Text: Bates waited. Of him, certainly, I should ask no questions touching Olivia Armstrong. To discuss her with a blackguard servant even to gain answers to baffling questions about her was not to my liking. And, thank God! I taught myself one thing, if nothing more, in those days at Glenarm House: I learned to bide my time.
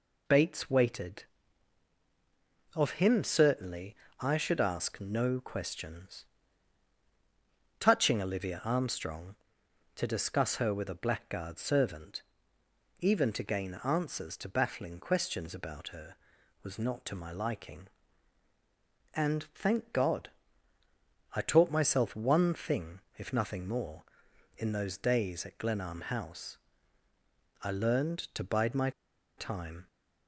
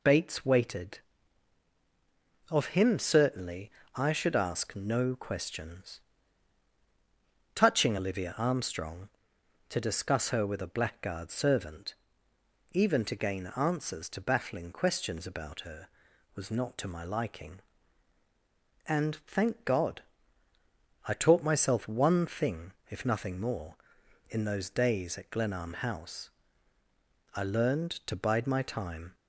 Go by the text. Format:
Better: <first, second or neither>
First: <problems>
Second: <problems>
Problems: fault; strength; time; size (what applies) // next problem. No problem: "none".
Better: second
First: pauses between "questions" and "touching"; strong; at 6.2 s; 1.5 s long // pauses between "servant" and "even"; noticeable; at 12.1 s; 0.80 s long // pauses between "my" and "time"; noticeable; at 28.8 s; 0.47 s long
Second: pauses between "questions" and "touching"; strong; at 5.9 s; 1.5 s long // pauses between "servant" and "even"; noticeable; at 11.9 s; 0.80 s long